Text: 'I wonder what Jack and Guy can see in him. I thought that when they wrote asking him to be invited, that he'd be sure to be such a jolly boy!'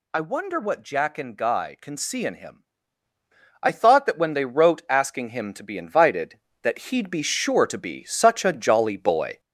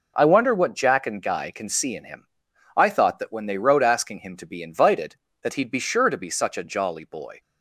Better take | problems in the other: second | gets louder; noticeable; throughout; 4 dB

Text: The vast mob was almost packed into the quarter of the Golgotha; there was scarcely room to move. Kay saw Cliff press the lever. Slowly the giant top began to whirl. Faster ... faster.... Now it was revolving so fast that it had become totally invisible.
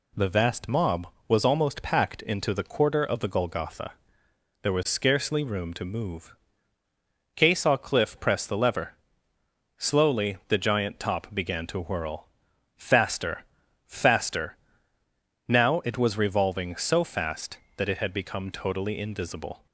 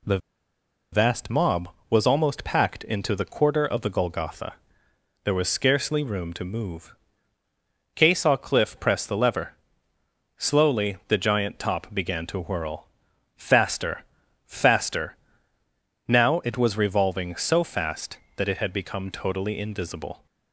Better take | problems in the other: first | pauses between "The" and "vast"; noticeable; at 0.1 s; 0.74 s long

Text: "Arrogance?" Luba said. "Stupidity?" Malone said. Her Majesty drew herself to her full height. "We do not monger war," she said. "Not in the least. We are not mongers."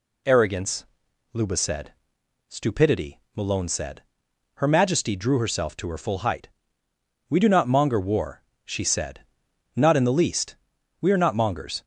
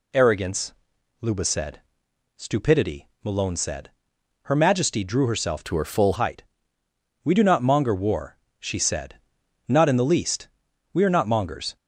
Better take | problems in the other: first | changes voice from "to" to "full"; from 5.6 to 6.1 s; 0.5 s long

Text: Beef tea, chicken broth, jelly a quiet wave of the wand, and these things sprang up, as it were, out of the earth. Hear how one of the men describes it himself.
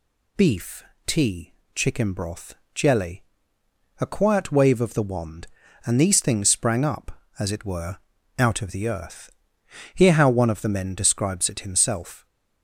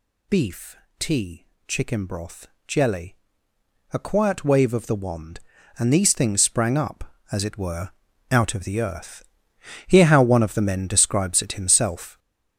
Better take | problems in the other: first | gets louder; throughout; 7 dB // pauses between "Beef" and "tea"; slight; at 0.7 s; 0.22 s long; slight in the first // pauses between "jelly" and "a"; noticeable; at 3.1 s; 0.76 s long; noticeable in the first

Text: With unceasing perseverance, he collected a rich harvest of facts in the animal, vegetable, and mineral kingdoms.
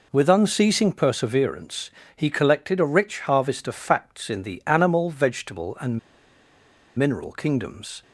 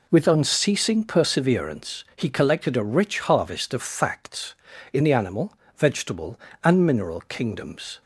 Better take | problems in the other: second | pauses between "and" and "mineral"; noticeable; at 5.9 s; 0.97 s long

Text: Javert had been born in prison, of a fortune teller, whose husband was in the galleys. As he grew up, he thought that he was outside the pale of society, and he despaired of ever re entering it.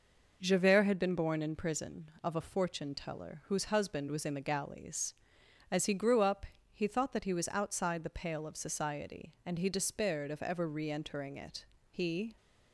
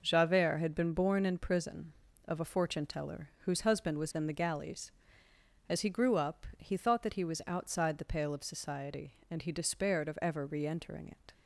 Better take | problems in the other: second | goes on to say "He"; slight; from 11.9 s on; 0.46 s long

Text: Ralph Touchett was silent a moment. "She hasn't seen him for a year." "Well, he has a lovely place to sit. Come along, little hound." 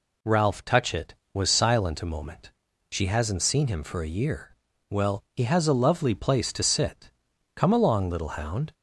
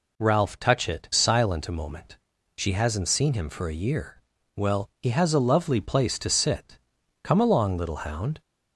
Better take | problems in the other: first | skips "was"; at 1.1 s

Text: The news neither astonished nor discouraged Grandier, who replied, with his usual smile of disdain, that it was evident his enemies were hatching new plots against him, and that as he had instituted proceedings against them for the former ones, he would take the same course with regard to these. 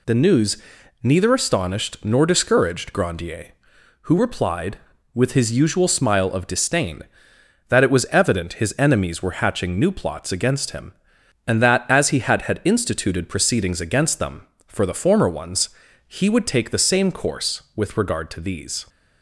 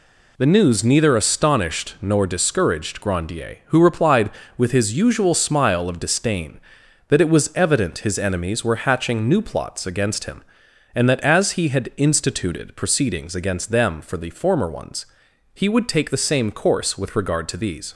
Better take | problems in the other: second | pauses between "news" and "neither"; noticeable; at 0.5 s; 0.46 s long // says "had" twice; at 12.4 s

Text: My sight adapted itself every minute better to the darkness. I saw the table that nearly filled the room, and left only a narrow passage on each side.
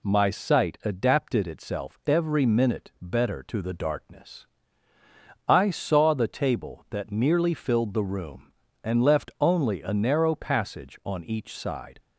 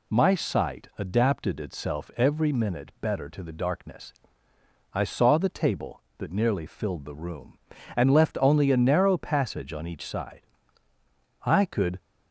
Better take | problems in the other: first | goes on to say "I could"; from 11.4 s on; 0.56 s long

